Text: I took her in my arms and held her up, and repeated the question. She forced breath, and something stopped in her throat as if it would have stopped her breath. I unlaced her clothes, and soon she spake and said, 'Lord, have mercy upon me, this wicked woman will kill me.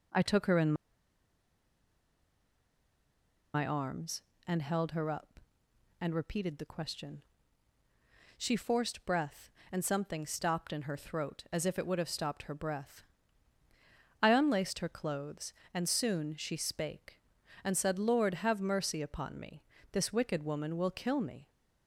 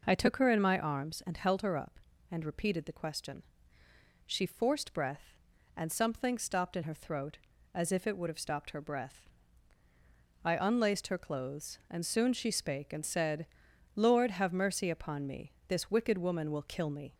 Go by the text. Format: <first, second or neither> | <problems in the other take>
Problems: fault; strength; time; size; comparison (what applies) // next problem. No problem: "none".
second | pauses between "in" and "my"; strong; at 0.7 s; 2.8 s long